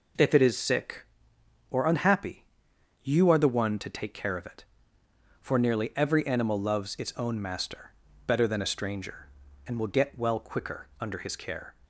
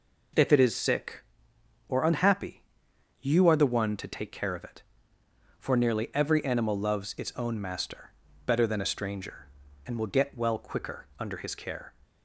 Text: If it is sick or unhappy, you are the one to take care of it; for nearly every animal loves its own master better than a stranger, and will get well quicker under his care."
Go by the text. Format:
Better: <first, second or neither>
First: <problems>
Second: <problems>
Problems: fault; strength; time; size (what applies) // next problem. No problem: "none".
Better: neither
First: pauses between "master" and "better"; slight; at 7.9 s; 0.34 s long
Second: pauses between "master" and "better"; slight; at 8.1 s; 0.34 s long